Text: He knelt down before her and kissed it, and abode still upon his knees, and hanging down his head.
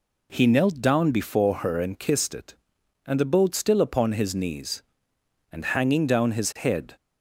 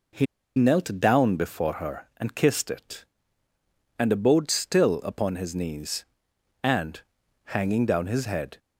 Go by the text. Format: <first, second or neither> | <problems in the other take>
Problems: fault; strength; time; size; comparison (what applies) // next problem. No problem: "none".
first | pauses between "He" and "knelt"; slight; at 0.2 s; 0.32 s long // pauses between "and" and "hanging"; noticeable; at 7.0 s; 0.46 s long